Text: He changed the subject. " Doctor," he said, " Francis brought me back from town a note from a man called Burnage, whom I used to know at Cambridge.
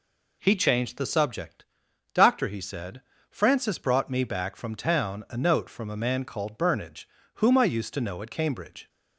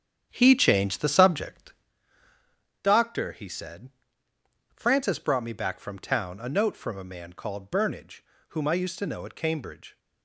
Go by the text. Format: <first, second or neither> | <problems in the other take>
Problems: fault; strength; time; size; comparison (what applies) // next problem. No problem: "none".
first | starts louder than the rest; strong; until 1.9 s; 8.5 dB